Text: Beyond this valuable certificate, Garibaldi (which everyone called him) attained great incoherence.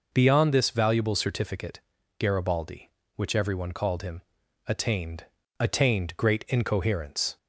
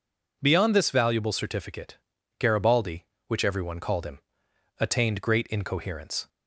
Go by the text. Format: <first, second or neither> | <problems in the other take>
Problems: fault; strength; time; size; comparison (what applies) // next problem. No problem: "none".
second | says "attained" twice; at 5.5 s